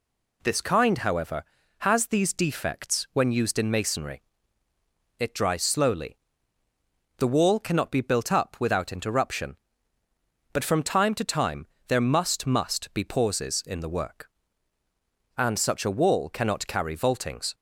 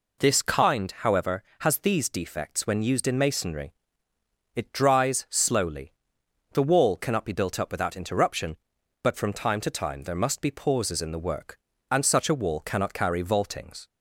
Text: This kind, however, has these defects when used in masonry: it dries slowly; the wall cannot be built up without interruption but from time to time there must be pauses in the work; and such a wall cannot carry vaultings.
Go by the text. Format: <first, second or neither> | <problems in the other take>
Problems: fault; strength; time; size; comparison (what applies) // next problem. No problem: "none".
second | pauses between "time" and "there"; slight; at 11.6 s; 0.22 s long // says "must" twice; at 12.4 s